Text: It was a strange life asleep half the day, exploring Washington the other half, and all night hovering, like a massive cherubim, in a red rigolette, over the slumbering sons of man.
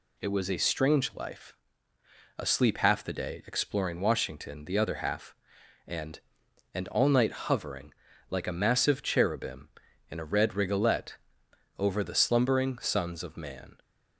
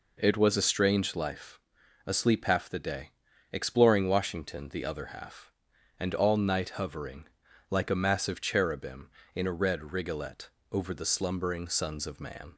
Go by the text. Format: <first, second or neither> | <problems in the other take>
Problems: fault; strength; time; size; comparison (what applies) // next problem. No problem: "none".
second | pauses between "life" and "asleep"; noticeable; at 1.5 s; 0.86 s long; also in the second // says "and" twice; at 6.7 s